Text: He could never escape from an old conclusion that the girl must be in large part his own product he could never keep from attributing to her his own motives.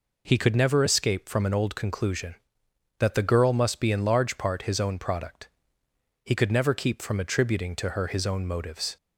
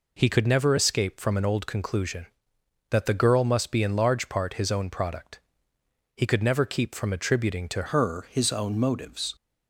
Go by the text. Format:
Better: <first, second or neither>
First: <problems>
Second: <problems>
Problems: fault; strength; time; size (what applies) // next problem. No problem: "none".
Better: first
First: pauses between "product" and "he"; noticeable; at 5.4 s; 0.78 s long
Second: pauses between "product" and "he"; noticeable; at 5.3 s; 0.78 s long // changes voice at "her"; from 7.9 s on; 1.4 s long